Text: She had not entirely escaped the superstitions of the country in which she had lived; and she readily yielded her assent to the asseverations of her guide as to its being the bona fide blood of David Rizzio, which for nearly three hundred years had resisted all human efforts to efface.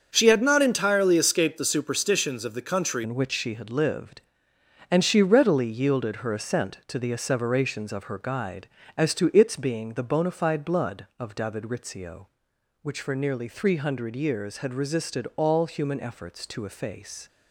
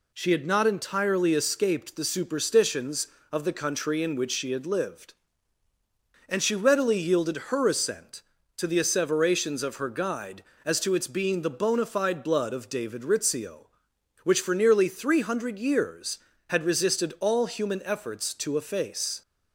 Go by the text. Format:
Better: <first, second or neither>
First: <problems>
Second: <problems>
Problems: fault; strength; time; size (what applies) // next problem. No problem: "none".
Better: second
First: starts louder than the rest; until 1.1 s; 7 dB // changes voice at "in"; from 3.0 s on; 14.2 s long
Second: none